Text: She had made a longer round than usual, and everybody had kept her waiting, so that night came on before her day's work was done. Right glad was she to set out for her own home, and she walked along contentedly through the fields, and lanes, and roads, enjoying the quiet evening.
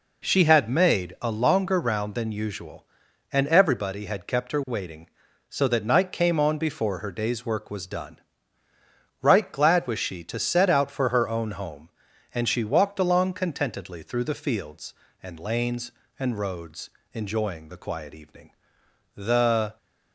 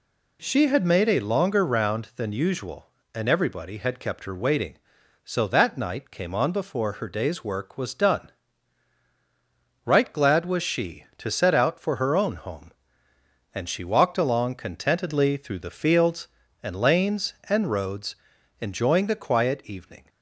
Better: second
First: goes on to say "The"; noticeable; from 19.1 s on; 0.62 s long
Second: none

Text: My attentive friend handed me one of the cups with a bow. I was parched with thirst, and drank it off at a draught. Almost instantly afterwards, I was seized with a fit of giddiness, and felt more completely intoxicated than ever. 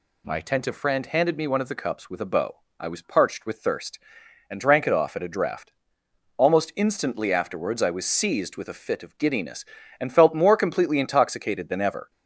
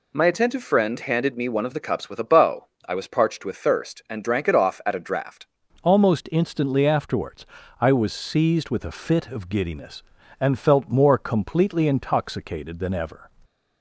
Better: first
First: none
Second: changes voice at "Almost"; from 5.8 s on; 7.4 s long

